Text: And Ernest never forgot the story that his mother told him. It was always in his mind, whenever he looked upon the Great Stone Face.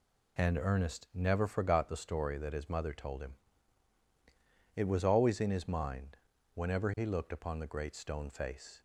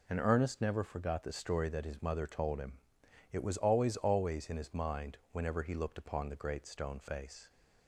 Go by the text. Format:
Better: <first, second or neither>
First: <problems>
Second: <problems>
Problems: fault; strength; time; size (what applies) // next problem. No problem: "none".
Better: first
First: none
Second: says "always" twice; at 3.9 s